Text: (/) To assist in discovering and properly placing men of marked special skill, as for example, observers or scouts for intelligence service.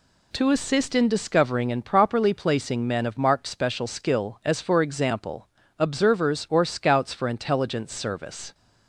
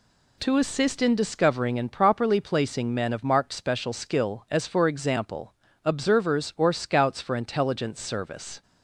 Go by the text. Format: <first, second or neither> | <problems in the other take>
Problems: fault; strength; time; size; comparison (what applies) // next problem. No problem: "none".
neither | none